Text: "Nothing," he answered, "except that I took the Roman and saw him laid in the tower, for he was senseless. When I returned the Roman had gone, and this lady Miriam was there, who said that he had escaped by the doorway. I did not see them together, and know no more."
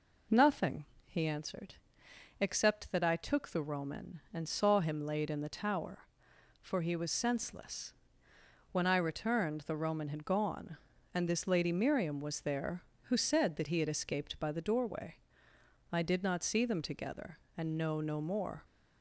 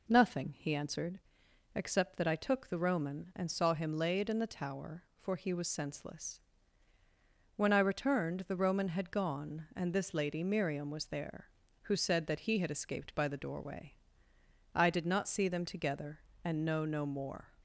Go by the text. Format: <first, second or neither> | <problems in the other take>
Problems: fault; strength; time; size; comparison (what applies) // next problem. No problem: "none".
neither | none